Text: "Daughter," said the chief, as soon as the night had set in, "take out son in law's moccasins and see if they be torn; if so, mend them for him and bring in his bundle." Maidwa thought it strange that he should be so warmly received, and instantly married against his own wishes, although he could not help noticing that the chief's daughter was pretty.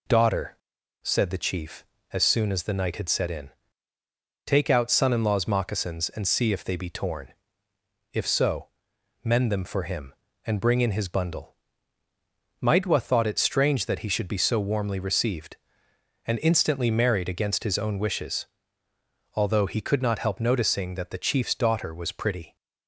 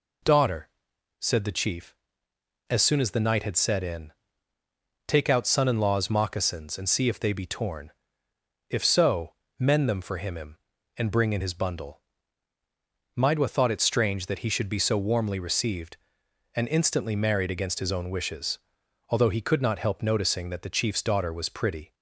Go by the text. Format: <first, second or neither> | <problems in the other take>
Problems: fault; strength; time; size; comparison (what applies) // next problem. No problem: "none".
first | says "him" twice; at 10.3 s